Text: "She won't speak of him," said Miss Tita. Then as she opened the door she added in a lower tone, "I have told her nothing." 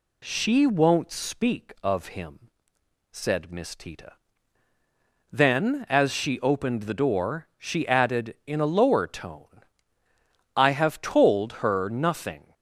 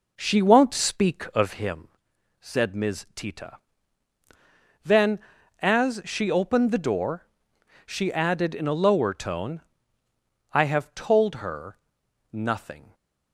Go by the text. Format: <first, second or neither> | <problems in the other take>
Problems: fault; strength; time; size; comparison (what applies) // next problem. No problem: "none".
first | starts louder than the rest; noticeable; until 1.7 s; 5 dB // pauses between "door" and "she"; noticeable; at 7.2 s; 0.58 s long // pauses between "her" and "nothing"; noticeable; at 11.7 s; 0.56 s long